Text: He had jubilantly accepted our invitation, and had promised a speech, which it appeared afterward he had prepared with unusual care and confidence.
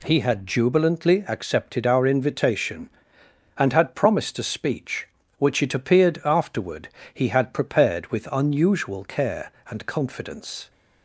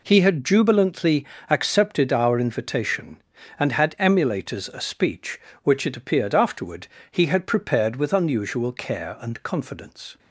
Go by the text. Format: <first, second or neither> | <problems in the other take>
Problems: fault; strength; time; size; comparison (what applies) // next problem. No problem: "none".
first | pauses between "jubilantly" and "accepted"; slight; at 1.2 s; 0.24 s long // says "emulators" for "promised"; at 3.9 s // pauses between "afterward" and "he"; slight; at 6.8 s; 0.22 s long; slight in the first